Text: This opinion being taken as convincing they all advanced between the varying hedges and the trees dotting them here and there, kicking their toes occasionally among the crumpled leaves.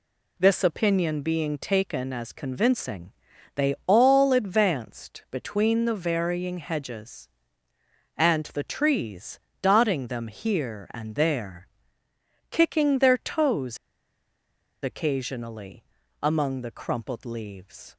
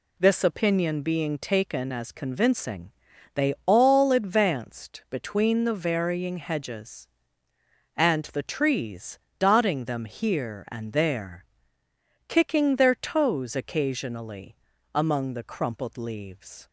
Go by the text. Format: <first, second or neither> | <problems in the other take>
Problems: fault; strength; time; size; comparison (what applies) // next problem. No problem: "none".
second | pauses between "convincing" and "they"; at 3.1 s; 0.42 s long; also in the second // pauses between "trees" and "dotting"; slight; at 9.4 s; 0.22 s long; slight in the second // pauses between "toes" and "occasionally"; at 13.7 s; 1.0 s long // pauses between "occasionally" and "among"; at 15.8 s; 0.38 s long; also in the second